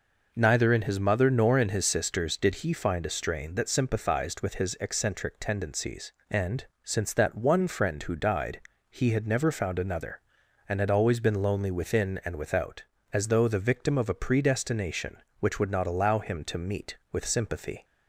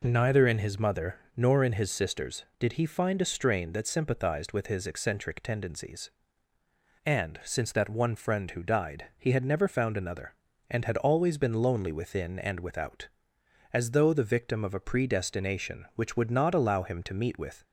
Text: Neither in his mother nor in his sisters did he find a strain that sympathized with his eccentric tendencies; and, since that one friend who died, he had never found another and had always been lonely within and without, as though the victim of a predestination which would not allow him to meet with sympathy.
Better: first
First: none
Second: pauses between "mother" and "nor"; slight; at 1.1 s; 0.20 s long // stops before "sympathy"; at 17.6 s

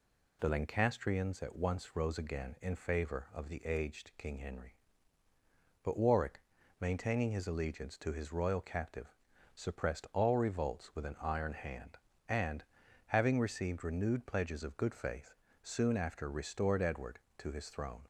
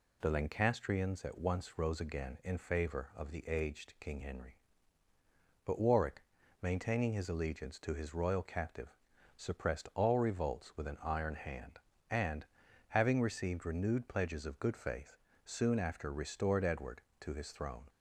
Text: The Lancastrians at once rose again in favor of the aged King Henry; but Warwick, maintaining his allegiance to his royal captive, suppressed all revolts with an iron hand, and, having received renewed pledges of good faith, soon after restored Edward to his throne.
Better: neither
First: none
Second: none

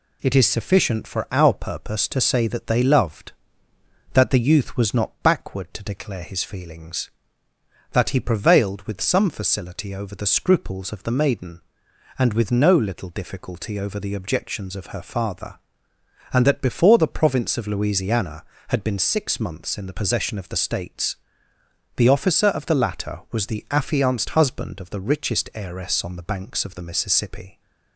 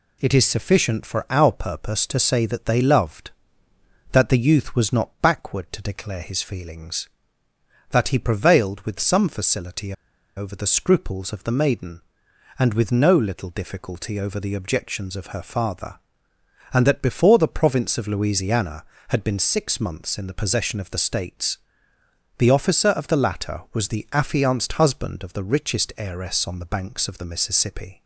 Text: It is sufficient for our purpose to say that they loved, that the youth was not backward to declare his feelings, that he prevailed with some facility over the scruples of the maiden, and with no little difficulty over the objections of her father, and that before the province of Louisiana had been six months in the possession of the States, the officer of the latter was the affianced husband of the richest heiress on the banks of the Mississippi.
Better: first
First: none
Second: pauses between "facility" and "over"; at 9.9 s; 0.43 s long

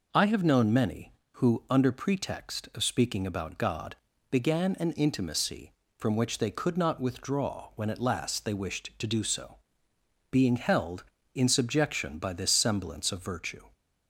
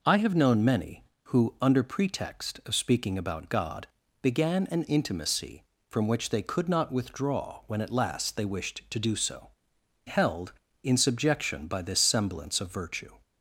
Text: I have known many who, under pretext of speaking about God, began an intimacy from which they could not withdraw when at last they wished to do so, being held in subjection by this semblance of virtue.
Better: first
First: none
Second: skips "being"; at 9.7 s

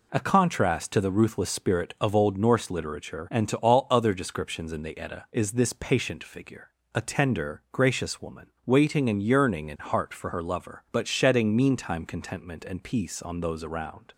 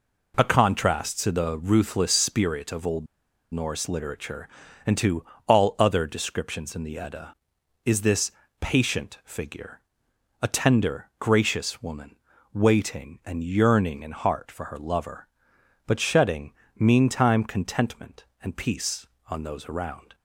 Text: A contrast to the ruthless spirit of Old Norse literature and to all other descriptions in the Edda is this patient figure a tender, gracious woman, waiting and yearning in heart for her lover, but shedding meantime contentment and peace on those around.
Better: first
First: pauses between "figure" and "a"; slight; at 6.7 s; 0.24 s long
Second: pauses between "Old" and "Norse"; noticeable; at 3.0 s; 0.46 s long // pauses between "to" and "all"; slight; at 5.2 s; 0.24 s long // pauses between "this" and "patient"; slight; at 8.3 s; 0.30 s long // pauses between "figure" and "a"; noticeable; at 9.8 s; 0.60 s long // pauses between "shedding" and "meantime"; slight; at 16.5 s; 0.24 s long

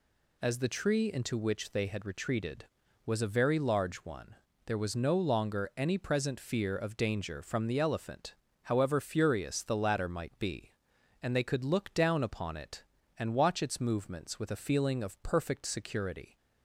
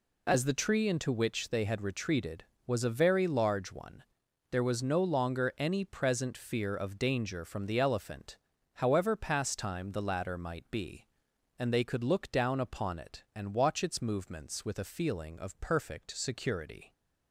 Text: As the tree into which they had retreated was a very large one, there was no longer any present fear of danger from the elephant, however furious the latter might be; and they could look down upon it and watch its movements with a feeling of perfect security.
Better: first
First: none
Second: says "pastime" for "furious"; at 9.1 s

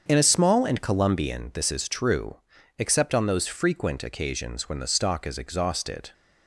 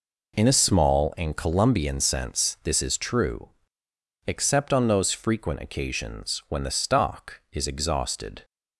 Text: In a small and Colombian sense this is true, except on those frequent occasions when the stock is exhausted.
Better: second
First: starts louder than the rest; until 1.0 s; 7 dB // skips "sense"; at 1.5 s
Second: none

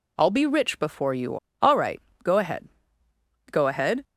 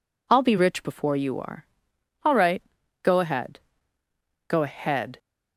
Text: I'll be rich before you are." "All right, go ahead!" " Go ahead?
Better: second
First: skips "are"; at 1.4 s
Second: none

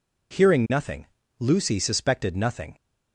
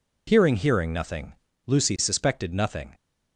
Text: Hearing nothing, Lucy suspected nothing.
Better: first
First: none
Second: says "Hearing" twice; at 0.5 s

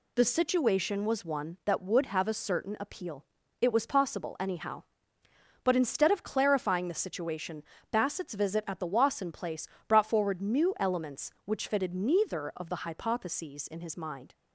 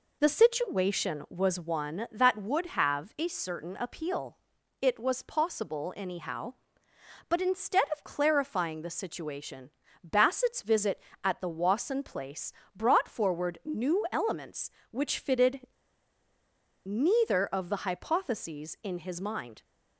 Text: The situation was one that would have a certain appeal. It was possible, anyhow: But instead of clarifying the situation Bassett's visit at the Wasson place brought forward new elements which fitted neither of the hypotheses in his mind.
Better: first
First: pauses between "situation" and "Bassett's"; slight; at 7.6 s; 0.30 s long // pauses between "place" and "brought"; slight; at 9.6 s; 0.20 s long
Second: pauses between "situation" and "Bassett's"; slight; at 9.7 s; 0.34 s long // pauses between "place" and "brought"; slight; at 12.5 s; 0.20 s long // pauses between "fitted" and "neither"; at 15.6 s; 1.1 s long

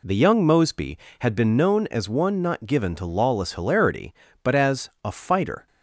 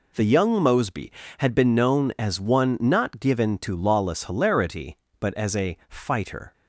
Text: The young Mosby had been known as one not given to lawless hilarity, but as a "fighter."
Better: neither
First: none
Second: none

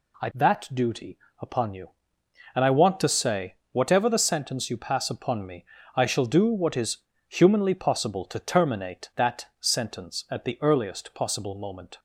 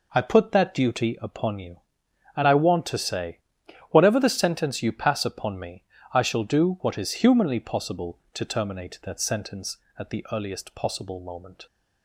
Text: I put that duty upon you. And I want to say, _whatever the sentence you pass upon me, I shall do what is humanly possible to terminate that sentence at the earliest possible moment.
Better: second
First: skips "put"; at 0.3 s // pauses between "duty" and "upon"; slight; at 1.1 s; 0.20 s long // pauses between "is" and "humanly"; slight; at 6.9 s; 0.30 s long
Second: none

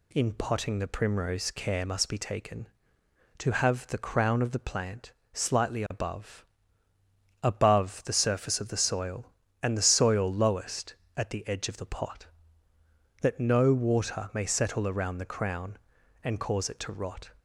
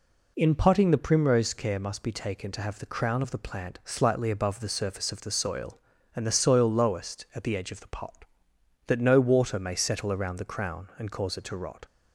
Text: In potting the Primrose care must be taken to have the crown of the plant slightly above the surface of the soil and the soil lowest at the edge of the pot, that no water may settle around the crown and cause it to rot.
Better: second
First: pauses between "plant" and "slightly"; slight; at 5.1 s; 0.18 s long // says "above" twice; at 7.4 s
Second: none

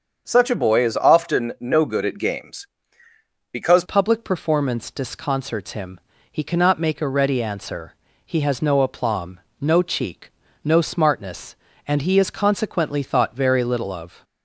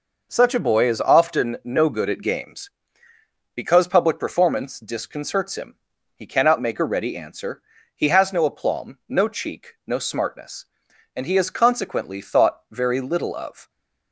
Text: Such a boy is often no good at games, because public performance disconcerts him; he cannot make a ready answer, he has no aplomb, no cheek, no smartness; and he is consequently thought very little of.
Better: second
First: starts louder than the rest; until 1.2 s; 7 dB // changes voice at "public"; from 3.8 s on; 10.4 s long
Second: none

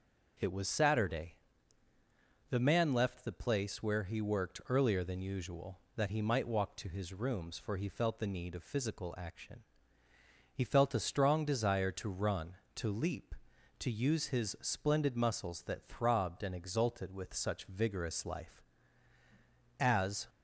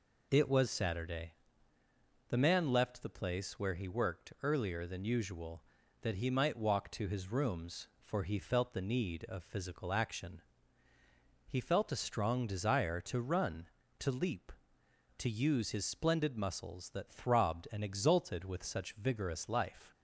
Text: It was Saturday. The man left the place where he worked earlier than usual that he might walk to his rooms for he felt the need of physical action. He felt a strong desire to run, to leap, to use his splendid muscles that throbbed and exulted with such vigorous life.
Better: second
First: starts louder than the rest; noticeable; until 2.5 s; 6 dB // goes on to say "As"; slight; from 19.7 s on; 0.48 s long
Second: none

